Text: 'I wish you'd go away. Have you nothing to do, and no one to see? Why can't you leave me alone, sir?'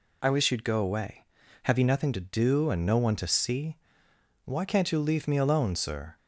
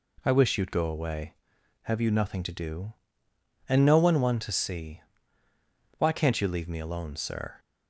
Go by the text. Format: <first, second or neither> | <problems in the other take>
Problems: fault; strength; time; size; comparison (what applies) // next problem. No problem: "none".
first | says "one" twice; at 4.1 s